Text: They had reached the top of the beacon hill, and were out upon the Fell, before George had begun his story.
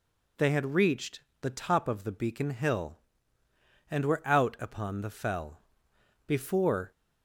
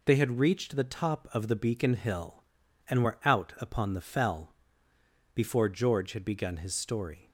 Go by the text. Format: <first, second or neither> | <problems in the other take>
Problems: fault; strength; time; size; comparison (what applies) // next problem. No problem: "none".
second | pauses between "reached" and "the"; slight; at 1.2 s; 0.21 s long // stops before "George had begun his story"; at 6.9 s